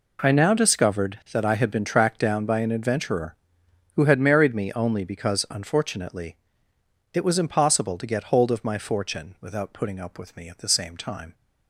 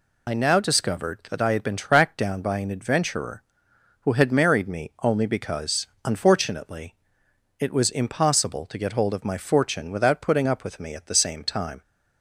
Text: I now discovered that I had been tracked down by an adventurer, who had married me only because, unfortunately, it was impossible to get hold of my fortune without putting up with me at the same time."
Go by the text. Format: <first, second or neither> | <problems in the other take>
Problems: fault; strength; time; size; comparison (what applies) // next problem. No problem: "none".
first | loses the start of "I"; at 0.2 s; 25 ms